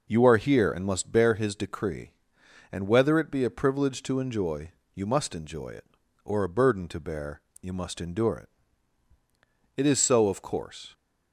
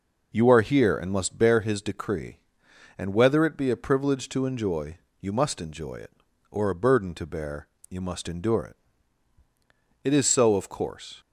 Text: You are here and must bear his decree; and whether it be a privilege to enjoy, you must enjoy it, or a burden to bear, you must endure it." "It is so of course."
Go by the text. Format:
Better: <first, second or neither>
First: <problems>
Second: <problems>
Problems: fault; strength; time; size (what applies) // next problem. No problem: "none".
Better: neither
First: none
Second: none